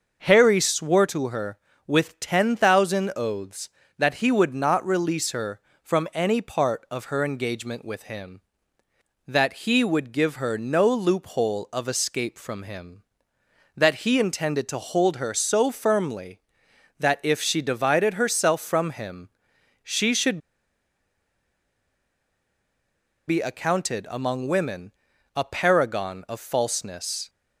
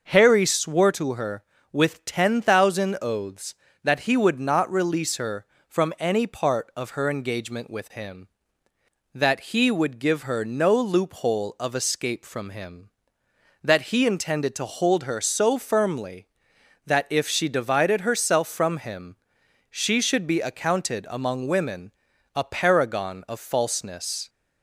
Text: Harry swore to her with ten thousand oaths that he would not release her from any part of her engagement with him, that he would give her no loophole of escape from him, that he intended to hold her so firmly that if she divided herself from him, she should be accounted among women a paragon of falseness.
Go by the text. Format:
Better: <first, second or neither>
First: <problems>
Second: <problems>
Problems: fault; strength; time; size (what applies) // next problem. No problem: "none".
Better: second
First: pauses between "should" and "be"; strong; at 20.3 s; 2.9 s long // pauses between "women" and "a"; at 24.9 s; 0.42 s long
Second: pauses between "women" and "a"; at 21.9 s; 0.42 s long